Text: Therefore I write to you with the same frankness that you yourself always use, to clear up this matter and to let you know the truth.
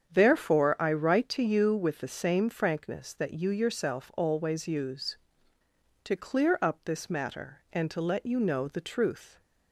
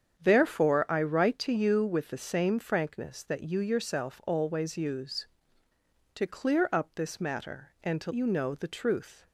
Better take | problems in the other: first | starts louder than the rest; strong; until 1.2 s; 8 dB; strong in the first // skips "let"; at 8.1 s

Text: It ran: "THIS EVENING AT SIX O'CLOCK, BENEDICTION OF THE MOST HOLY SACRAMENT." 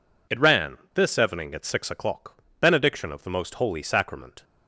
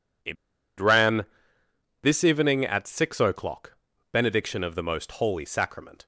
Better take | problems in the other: first | pauses between "It" and "ran"; at 0.3 s; 0.43 s long

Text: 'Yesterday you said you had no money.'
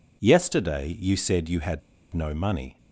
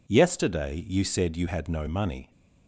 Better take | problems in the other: second | pauses between "had" and "no"; slight; at 1.7 s; 0.34 s long

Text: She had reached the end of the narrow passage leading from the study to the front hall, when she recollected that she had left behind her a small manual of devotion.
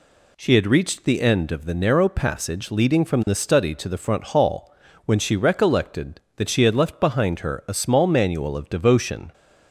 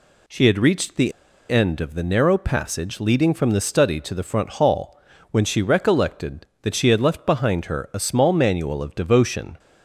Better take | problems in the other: first | pauses between "the" and "end"; at 1.1 s; 0.38 s long

